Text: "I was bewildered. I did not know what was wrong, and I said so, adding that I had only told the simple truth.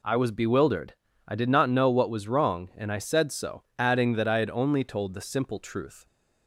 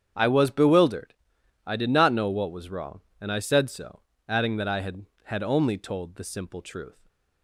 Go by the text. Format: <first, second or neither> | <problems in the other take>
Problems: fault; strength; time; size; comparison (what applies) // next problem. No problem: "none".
first | starts louder than the rest; strong; until 1.6 s; 8.5 dB // says "had" twice; at 5.2 s // stays silent after the last word; slight; from 6.9 s on; 0.5 s long